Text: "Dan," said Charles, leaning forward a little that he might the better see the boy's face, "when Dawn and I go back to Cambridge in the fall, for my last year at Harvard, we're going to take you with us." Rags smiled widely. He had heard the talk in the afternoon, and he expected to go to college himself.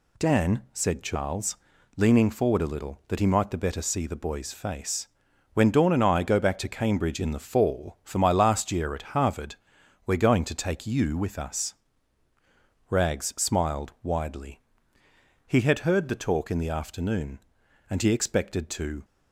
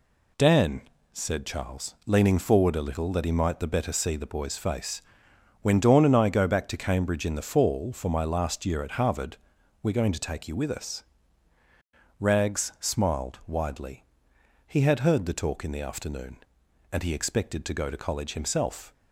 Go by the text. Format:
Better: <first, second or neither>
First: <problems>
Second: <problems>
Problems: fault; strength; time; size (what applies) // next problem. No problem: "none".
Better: second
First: stops before "go to college himself"; at 19.0 s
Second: none